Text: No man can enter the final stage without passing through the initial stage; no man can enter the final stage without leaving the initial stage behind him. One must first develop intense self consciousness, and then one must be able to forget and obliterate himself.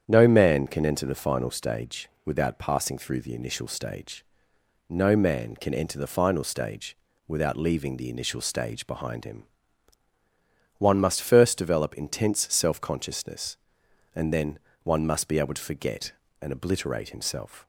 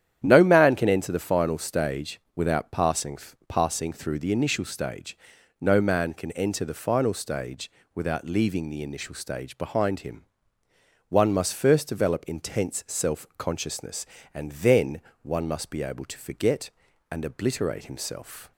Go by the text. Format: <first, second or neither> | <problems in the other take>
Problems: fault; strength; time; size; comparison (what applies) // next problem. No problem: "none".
first | starts louder than the rest; strong; until 1.2 s; 10.5 dB; strong in the first // pauses between "stage" and "without"; slight; at 2.1 s; 0.16 s long; slight in the first // says "passing" twice; at 3.4 s // pauses between "stage" and "without"; slight; at 7.7 s; 0.24 s long; slight in the first // pauses between "then" and "one"; slight; at 14.9 s; 0.24 s long; slight in the first